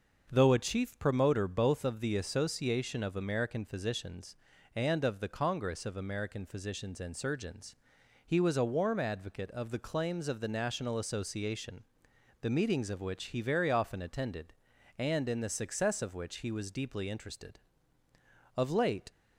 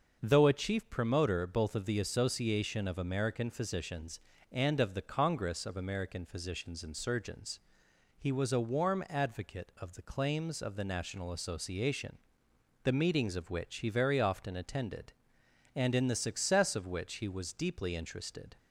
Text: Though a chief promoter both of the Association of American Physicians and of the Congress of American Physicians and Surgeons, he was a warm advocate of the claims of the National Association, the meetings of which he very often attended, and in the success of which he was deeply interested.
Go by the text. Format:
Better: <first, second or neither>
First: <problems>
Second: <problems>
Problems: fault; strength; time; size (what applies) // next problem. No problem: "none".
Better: second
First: starts louder than the rest; noticeable; until 1.3 s; 6 dB // goes on to say "Of late"; from 18.5 s on; 0.56 s long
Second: starts louder than the rest; until 1.2 s; 6 dB